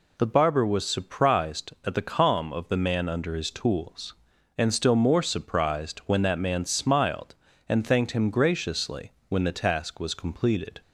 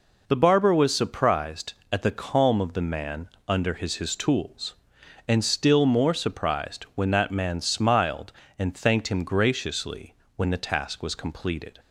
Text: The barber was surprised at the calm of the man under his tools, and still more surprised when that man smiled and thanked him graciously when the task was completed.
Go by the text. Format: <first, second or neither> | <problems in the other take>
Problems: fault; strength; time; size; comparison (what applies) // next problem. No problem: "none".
first | pauses between "man" and "under"; slight; at 3.2 s; 0.20 s long // says "his" twice; at 3.9 s // pauses between "graciously" and "when"; slight; at 10.1 s; 0.20 s long; slight in the first